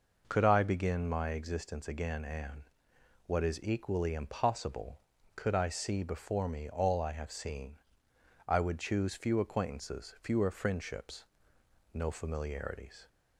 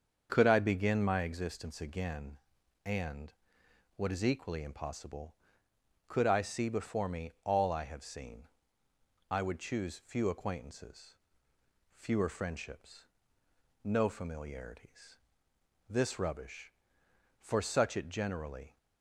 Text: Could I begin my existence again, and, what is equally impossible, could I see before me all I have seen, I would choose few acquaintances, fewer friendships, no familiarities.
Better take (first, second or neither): first